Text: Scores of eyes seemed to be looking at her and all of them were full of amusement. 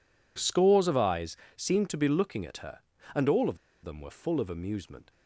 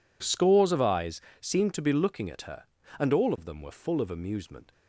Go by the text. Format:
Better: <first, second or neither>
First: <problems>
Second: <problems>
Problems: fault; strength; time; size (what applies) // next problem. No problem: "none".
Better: second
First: pauses between "eyes" and "seemed"; slight; at 1.3 s; 0.20 s long // pauses between "of" and "them"; slight; at 3.5 s; 0.26 s long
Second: pauses between "eyes" and "seemed"; slight; at 1.1 s; 0.20 s long